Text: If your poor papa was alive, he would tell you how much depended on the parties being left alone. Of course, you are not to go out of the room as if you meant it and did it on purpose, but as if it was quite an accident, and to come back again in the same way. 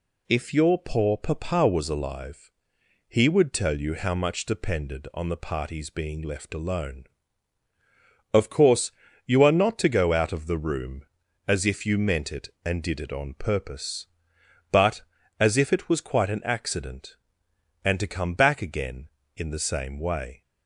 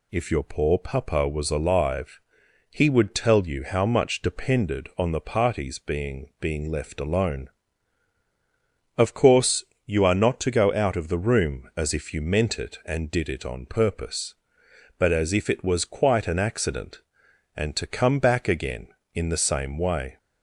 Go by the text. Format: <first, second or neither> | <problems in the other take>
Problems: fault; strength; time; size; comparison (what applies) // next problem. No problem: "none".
first | says "being" twice; at 6.3 s